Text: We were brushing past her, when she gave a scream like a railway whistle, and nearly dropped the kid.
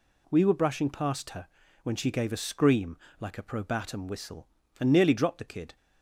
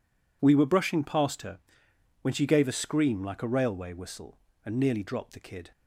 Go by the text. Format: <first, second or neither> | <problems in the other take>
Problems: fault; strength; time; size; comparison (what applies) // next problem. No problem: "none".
second | pauses between "scream" and "like"; slight; at 2.9 s; 0.22 s long // says "probatum" for "railway"; at 3.4 s